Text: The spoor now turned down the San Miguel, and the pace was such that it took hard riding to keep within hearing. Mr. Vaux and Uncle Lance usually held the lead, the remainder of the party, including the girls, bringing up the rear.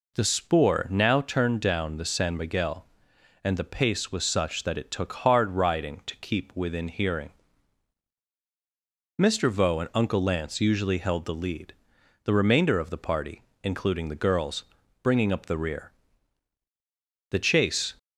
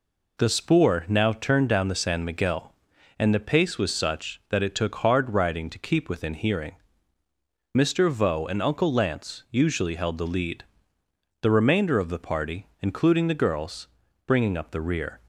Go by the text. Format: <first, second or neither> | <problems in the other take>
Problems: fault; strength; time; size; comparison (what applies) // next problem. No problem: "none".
second | goes on to say "The chase"; noticeable; from 17.2 s on; 0.64 s long